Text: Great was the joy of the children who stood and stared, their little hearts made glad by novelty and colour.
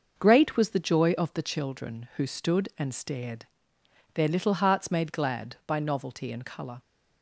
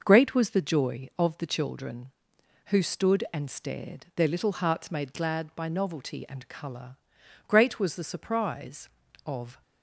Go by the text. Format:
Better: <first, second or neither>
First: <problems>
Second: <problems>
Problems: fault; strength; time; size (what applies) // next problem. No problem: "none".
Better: first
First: none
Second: goes on to say "Great was the surprise of"; strong; from 7.4 s on; 2.1 s long